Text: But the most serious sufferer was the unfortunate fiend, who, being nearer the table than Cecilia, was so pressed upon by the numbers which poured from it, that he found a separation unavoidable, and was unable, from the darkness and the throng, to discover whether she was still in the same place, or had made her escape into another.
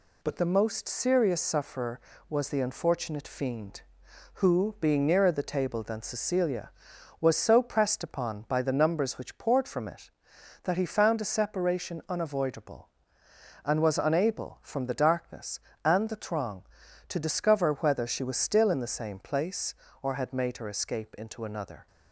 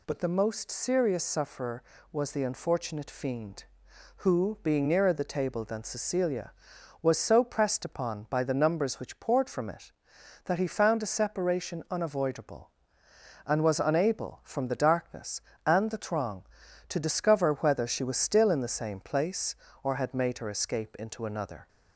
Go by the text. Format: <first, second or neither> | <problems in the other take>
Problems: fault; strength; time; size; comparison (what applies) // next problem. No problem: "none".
second | gets quieter; throughout; 4 dB